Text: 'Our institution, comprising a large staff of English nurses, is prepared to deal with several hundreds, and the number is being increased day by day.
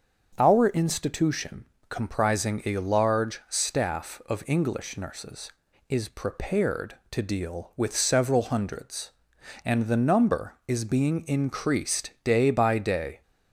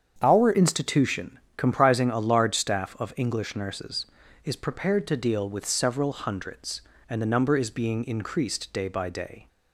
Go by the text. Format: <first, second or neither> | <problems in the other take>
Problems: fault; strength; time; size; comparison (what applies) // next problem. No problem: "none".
first | starts louder than the rest; strong; until 1.2 s; 7.5 dB; also in the first // changes voice at "institution"; from 0.5 s on; 8.9 s long